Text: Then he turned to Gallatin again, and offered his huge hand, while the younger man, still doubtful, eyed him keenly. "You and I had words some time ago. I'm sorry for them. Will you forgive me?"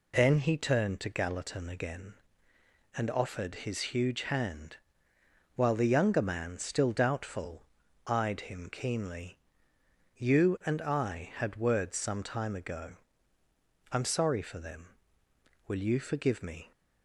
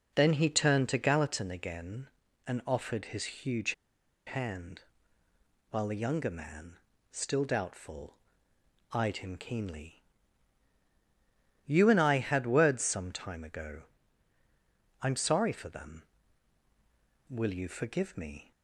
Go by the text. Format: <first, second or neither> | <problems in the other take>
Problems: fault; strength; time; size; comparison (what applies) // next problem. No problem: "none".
first | pauses between "huge" and "hand"; noticeable; at 3.7 s; 0.53 s long